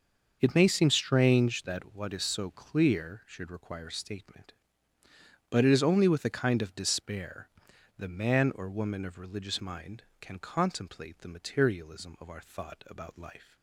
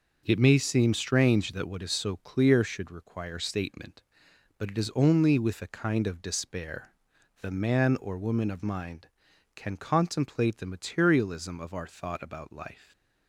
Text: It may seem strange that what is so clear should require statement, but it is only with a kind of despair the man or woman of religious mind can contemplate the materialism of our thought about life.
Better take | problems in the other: first | starts louder than the rest; noticeable; until 1.2 s; 6 dB; also in the first // pauses between "despair" and "the"; noticeable; at 6.9 s; 0.52 s long; noticeable in the first // skips "religious"; at 8.6 s

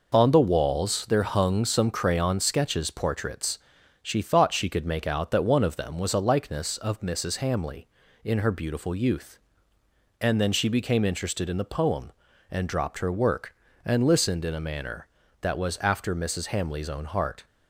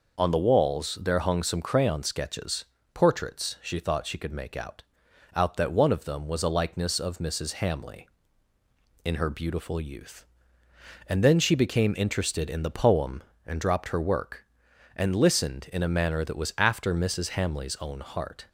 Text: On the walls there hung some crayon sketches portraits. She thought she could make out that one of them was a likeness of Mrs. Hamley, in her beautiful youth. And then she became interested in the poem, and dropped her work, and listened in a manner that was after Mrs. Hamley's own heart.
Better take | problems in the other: first | pauses between "sketches" and "portraits"; slight; at 2.6 s; 0.28 s long // says "out" twice; at 5.3 s

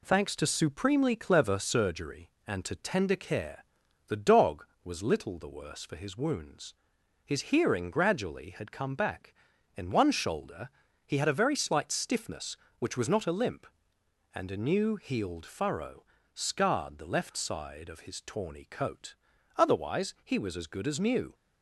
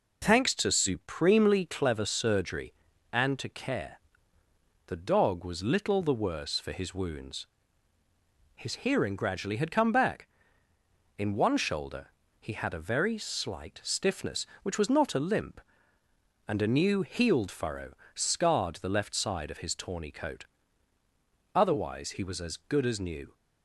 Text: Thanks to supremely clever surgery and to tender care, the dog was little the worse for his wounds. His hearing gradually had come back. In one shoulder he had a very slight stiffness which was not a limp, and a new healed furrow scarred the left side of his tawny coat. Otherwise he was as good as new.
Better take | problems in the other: first | skips "tender"; at 3.4 s // pauses between "shoulder" and "he"; slight; at 12.0 s; 0.32 s long; also in the first // pauses between "furrow" and "scarred"; slight; at 17.9 s; 0.24 s long; slight in the first

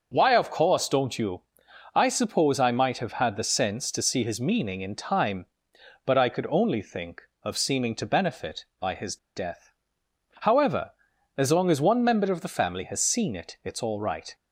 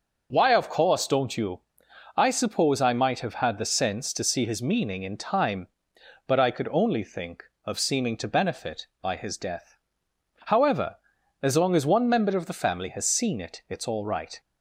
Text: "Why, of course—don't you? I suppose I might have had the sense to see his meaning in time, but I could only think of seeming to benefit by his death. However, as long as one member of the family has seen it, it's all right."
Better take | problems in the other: second | pauses between "his" and "death"; slight; at 9.1 s; 0.19 s long

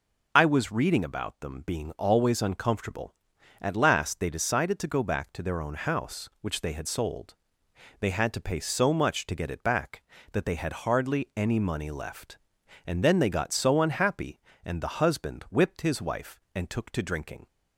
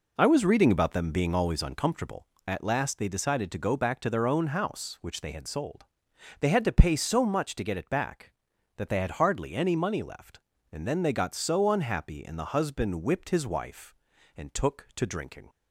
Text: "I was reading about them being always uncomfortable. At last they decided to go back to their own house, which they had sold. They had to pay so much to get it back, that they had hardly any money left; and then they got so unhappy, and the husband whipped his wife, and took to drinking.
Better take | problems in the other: neither | none

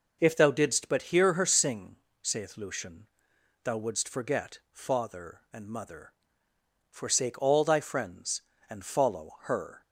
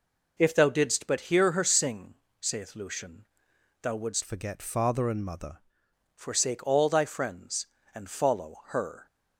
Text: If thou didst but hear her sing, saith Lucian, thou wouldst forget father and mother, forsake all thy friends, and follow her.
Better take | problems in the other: first | changes voice from "forget" to "mother"; from 4.2 to 5.5 s; 1.3 s long

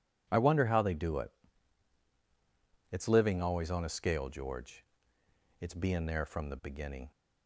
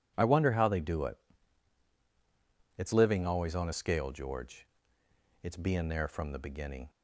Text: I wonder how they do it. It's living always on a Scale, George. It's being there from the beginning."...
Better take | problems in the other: neither | none

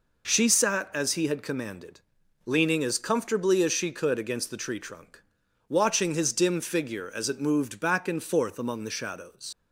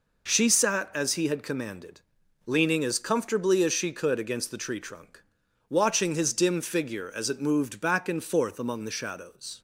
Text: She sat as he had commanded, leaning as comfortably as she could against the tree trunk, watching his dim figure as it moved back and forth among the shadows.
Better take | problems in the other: second | leaves "shadows" unfinished; at 9.5 s; 70 ms

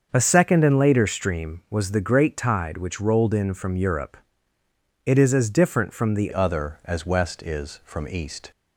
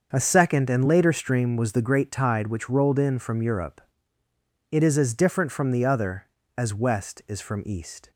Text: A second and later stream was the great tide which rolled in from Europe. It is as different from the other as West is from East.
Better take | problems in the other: second | starts louder than the rest; until 1.1 s; 7 dB; also in the second // changes voice at "other"; from 6.3 s on; 2.2 s long

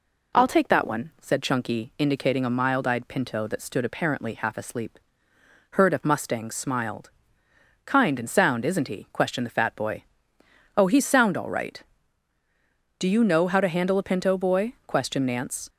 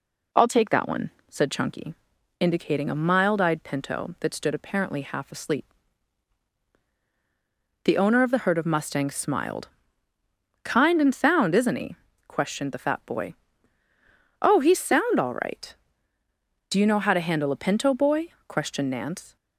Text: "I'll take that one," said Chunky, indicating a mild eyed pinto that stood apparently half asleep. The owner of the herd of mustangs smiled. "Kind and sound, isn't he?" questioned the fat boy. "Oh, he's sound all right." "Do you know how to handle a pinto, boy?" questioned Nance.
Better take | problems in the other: second | skips "The owner of the"; at 5.3 s

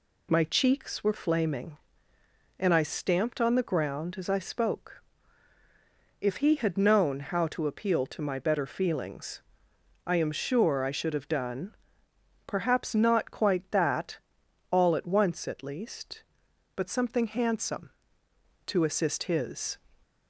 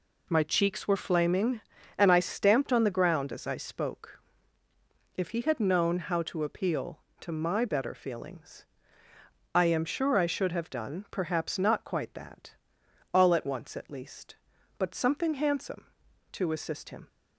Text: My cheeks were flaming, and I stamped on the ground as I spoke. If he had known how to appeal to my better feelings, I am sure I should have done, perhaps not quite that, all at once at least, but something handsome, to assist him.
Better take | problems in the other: second | says "his" for "him"; at 19.2 s

